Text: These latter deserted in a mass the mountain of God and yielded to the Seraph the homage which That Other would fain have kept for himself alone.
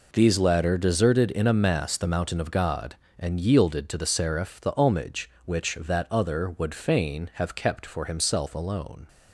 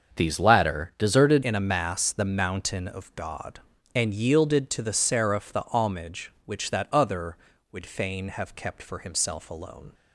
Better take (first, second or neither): first